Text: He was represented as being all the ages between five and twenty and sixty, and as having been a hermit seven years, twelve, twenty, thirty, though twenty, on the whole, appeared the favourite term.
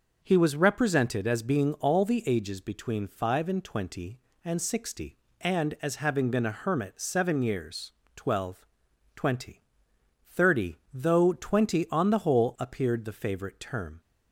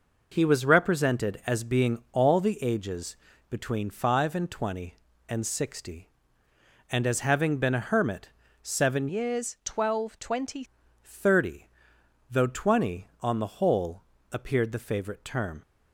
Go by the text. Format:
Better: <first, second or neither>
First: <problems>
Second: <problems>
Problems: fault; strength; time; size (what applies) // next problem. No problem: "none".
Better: first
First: none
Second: pauses between "ages" and "between"; slight; at 3.1 s; 0.34 s long // pauses between "hermit" and "seven"; slight; at 8.3 s; 0.32 s long // changes voice from "years" to "twenty"; from 9.0 to 10.6 s; 1.6 s long